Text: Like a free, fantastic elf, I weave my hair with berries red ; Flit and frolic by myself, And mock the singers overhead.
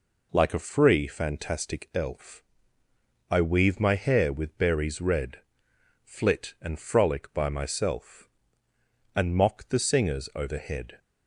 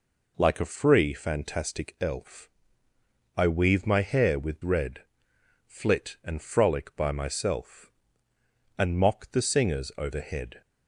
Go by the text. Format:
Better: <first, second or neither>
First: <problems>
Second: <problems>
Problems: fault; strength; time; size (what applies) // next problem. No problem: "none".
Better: first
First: none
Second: skips "berries"; at 4.6 s